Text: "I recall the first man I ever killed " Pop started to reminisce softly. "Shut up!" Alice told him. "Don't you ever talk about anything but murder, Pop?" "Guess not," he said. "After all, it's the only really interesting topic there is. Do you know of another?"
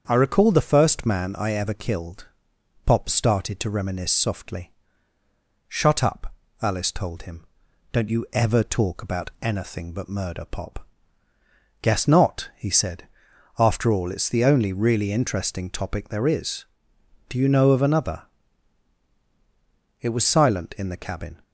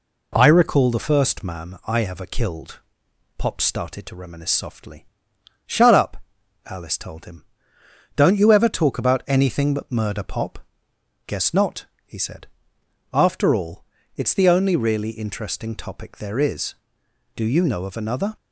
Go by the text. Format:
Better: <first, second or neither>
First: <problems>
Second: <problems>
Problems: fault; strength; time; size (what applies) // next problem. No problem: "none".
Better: second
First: starts louder than the rest; until 1.0 s; 7 dB // goes on to say "It was silent in the cabin"; from 20.0 s on; 1.4 s long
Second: none